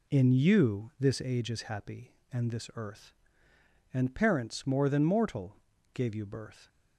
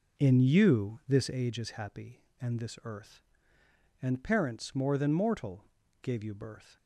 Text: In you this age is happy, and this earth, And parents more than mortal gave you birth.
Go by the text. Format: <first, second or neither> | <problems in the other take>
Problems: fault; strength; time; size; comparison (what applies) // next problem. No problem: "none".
first | starts louder than the rest; noticeable; until 1.6 s; 4.5 dB // pauses between "mortal" and "gave"; at 5.6 s; 0.38 s long; also in the first